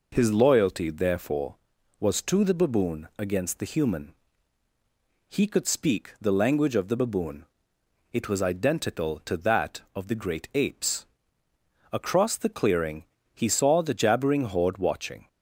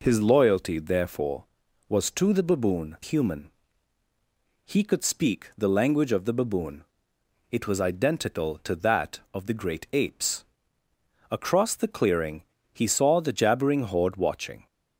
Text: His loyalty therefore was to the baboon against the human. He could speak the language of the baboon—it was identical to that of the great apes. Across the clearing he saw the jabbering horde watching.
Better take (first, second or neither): first